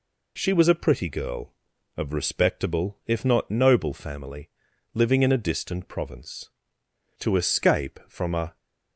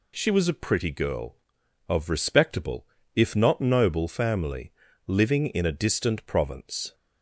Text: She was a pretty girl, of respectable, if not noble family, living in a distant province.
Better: second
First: goes on to say "To escape from a"; from 7.1 s on; 1.4 s long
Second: none

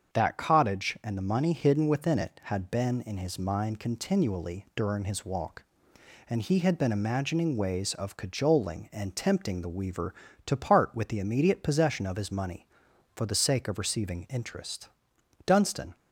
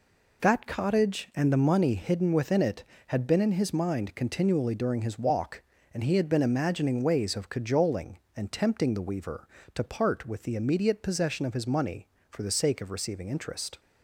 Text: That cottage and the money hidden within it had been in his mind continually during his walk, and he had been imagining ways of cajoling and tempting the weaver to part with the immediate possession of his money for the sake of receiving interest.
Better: second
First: starts louder than the rest; strong; until 1.1 s; 7 dB // goes on to say "Dunstan"; from 15.4 s on; 0.50 s long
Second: none

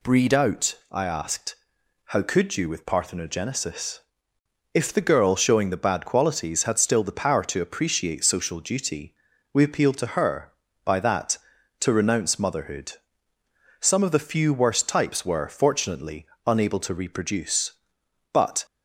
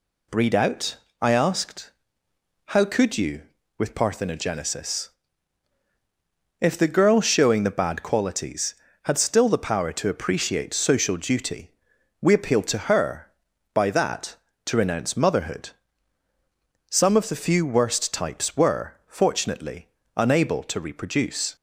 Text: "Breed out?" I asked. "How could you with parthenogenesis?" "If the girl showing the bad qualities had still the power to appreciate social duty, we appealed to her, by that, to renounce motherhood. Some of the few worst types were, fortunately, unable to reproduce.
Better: second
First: goes on to say "But"; slight; from 18.3 s on; 0.32 s long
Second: none

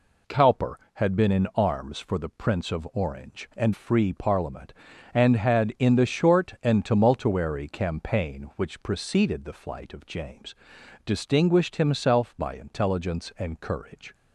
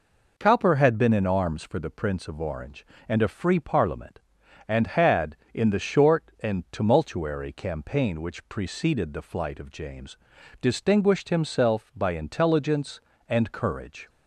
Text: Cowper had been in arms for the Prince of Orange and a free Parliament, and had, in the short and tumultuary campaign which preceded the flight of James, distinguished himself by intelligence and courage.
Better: second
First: skips "a"; at 3.7 s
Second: none

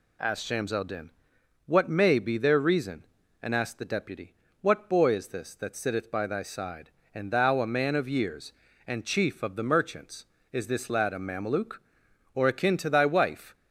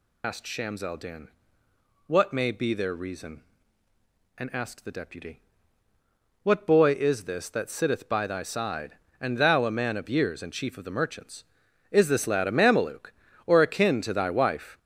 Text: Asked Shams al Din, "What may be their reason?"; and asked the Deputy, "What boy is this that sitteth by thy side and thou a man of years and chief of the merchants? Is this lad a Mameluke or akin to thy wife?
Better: first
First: none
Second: loses the start of "Asked"; at 0.2 s; 65 ms

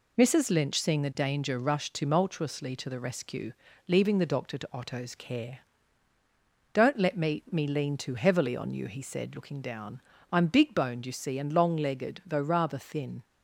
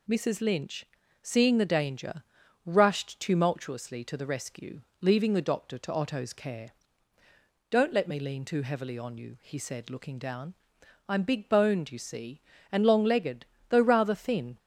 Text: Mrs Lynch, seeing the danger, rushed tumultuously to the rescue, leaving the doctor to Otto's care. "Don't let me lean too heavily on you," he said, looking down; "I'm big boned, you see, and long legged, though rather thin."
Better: second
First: says "me" twice; at 7.4 s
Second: none

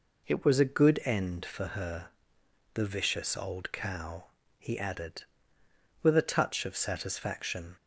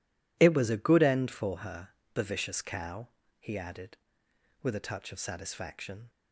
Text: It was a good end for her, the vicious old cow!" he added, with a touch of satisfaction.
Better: first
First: none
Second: skips "old"; at 2.6 s

